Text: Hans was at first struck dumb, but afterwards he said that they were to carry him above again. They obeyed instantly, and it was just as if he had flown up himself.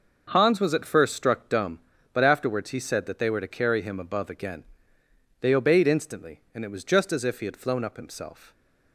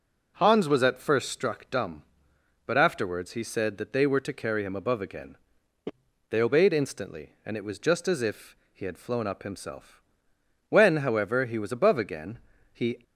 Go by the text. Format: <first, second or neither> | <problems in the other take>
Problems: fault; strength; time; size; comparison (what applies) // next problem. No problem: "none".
first | pauses between "if" and "he"; slight; at 8.5 s; 0.16 s long // goes on to say "When however he was above again he"; strong; from 10.6 s on; 2.3 s long